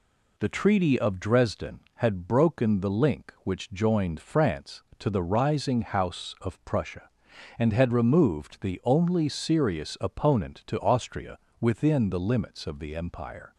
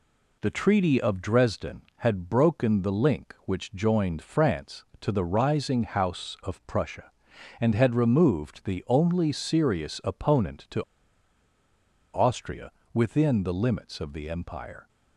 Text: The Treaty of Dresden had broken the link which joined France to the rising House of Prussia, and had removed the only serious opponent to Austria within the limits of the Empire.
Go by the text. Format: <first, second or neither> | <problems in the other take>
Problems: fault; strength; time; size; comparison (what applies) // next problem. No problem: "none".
first | pauses between "to" and "Austria"; strong; at 10.8 s; 1.3 s long // pauses between "Austria" and "within"; slight; at 12.7 s; 0.22 s long; slight in the first